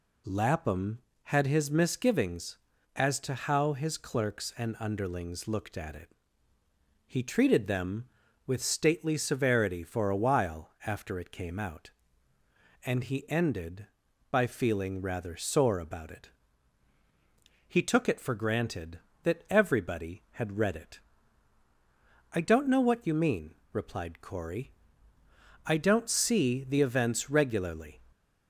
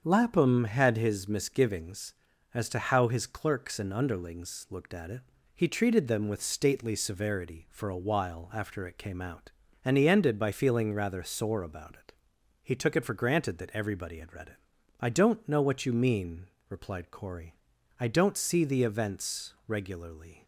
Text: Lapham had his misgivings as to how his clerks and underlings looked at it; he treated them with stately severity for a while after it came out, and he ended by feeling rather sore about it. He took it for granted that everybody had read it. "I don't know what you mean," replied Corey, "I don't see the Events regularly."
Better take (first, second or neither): first